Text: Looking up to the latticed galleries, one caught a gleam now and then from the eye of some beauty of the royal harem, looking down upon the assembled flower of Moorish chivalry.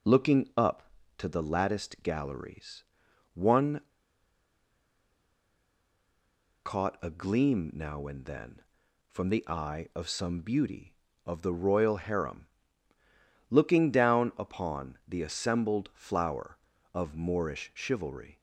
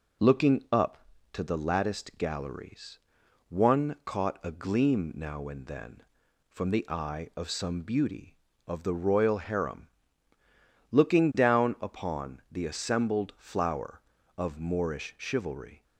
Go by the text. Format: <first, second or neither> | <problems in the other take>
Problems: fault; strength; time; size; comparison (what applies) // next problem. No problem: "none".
second | pauses between "one" and "caught"; strong; at 3.8 s; 2.8 s long